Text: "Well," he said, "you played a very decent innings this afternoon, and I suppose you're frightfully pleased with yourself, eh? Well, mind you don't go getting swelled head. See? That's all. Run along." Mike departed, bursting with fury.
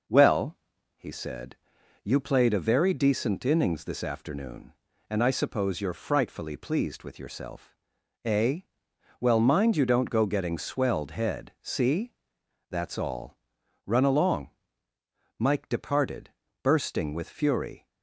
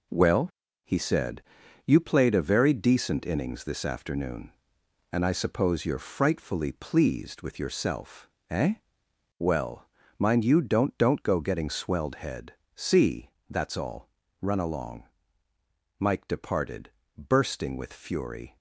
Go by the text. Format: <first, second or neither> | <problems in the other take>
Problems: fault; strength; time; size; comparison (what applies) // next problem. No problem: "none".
first | says "don't" twice; at 10.9 s